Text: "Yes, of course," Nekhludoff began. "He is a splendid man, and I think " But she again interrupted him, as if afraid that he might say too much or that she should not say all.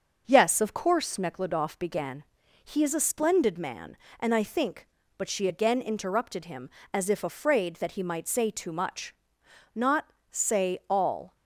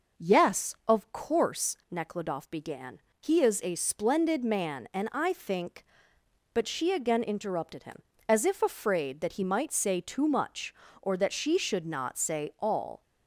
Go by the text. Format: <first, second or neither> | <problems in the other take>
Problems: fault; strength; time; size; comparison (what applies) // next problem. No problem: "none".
second | starts louder than the rest; until 1.2 s; 6.5 dB // skips "or that she should"; at 9.4 s // pauses between "not" and "say"; slight; at 10.1 s; 0.18 s long